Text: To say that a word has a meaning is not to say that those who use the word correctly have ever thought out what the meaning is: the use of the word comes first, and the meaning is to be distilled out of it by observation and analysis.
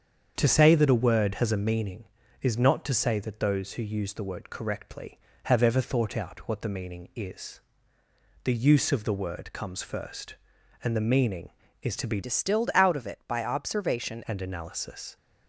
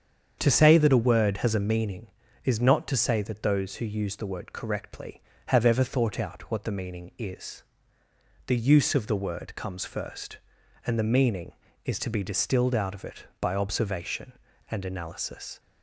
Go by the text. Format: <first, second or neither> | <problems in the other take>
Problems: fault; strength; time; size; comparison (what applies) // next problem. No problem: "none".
second | starts louder than the rest; strong; until 1.3 s; 7.5 dB; strong in the second // changes voice from "distilled" to "observation"; from 12.2 to 14.2 s; 2.0 s long